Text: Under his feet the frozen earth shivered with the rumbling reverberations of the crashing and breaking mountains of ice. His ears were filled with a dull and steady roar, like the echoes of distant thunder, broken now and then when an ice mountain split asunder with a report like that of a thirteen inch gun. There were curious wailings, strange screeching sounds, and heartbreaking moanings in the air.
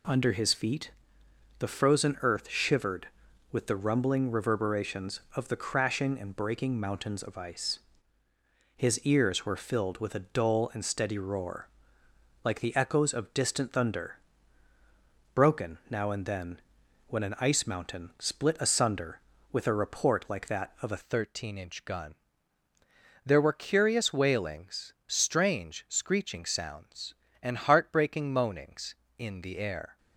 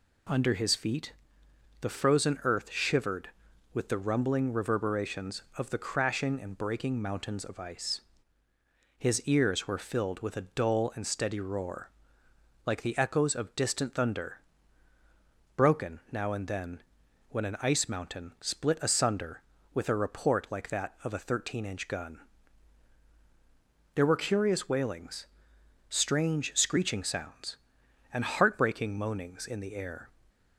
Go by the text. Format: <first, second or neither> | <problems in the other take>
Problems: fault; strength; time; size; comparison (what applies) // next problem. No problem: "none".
second | pauses between "feet" and "the"; noticeable; at 0.9 s; 0.66 s long; noticeable in the second // pauses between "then" and "when"; noticeable; at 16.5 s; 0.48 s long; noticeable in the second // changes voice at "thirteen"; from 21.0 s on; 8.9 s long